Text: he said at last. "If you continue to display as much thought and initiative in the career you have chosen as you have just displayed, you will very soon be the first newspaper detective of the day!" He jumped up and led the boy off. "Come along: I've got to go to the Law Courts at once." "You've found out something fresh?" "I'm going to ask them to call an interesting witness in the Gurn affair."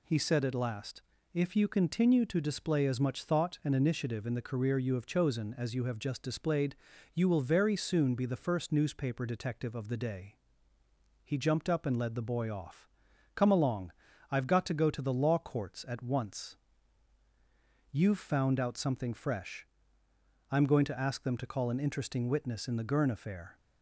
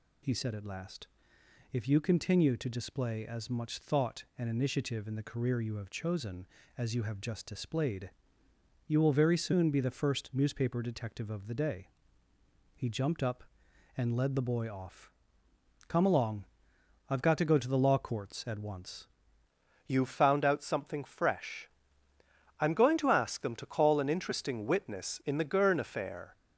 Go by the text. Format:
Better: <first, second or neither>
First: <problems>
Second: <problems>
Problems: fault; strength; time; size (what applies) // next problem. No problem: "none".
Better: first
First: none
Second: changes voice at "You've"; from 19.8 s on; 6.5 s long